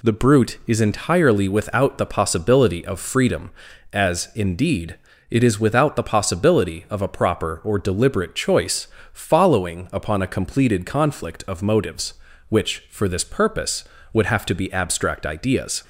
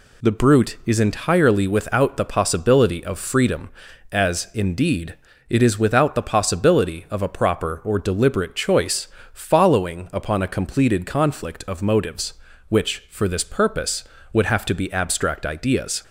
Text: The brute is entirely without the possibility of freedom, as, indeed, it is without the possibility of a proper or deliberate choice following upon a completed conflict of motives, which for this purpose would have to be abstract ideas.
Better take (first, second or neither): neither